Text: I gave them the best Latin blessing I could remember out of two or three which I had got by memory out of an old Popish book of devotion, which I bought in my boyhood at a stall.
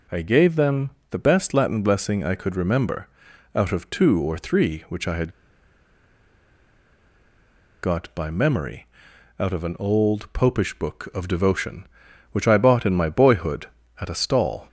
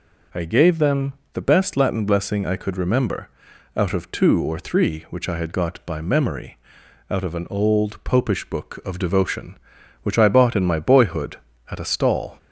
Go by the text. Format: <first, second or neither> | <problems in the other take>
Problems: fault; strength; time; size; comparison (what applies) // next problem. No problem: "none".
second | pauses between "them" and "the"; slight; at 0.9 s; 0.18 s long; slight in the second // pauses between "remember" and "out"; noticeable; at 3.0 s; 0.46 s long; noticeable in the second // pauses between "had" and "got"; strong; at 5.3 s; 2.5 s long // pauses between "memory" and "out"; noticeable; at 8.8 s; 0.52 s long; noticeable in the second